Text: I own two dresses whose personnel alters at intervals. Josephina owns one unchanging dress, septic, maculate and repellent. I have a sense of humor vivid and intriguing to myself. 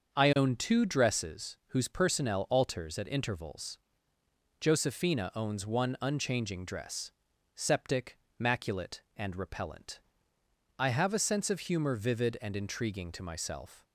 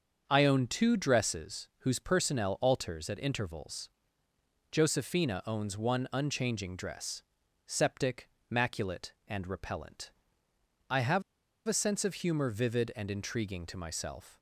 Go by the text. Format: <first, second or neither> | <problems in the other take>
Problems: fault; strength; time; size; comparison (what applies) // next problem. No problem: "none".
first | starts louder than the rest; until 1.2 s; 6.5 dB; also in the first // pauses between "have" and "a"; noticeable; at 11.2 s; 0.46 s long